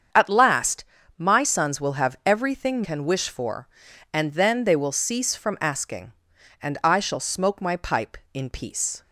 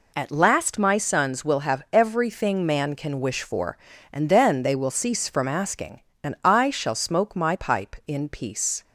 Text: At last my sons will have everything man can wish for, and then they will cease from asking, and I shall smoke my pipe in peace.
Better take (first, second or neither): second